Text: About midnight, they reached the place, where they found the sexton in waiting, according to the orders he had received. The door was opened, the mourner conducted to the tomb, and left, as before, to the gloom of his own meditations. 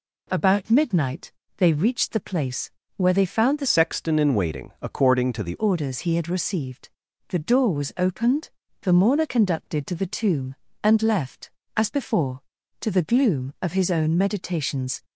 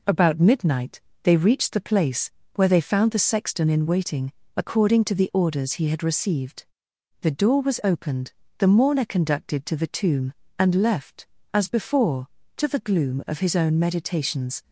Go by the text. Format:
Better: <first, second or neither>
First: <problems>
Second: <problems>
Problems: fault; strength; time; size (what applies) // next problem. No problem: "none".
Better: second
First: changes voice from "sexton" to "the"; from 3.6 to 5.5 s; 1.9 s long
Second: none